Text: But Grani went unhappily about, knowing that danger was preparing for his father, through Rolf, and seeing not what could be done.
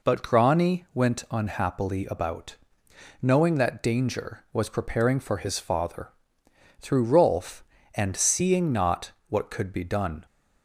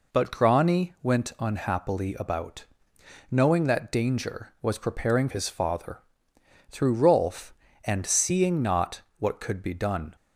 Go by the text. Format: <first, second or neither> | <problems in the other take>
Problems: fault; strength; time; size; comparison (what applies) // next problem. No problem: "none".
first | skips "for"; at 5.2 s // pauses between "not" and "what"; slight; at 9.0 s; 0.18 s long; slight in the first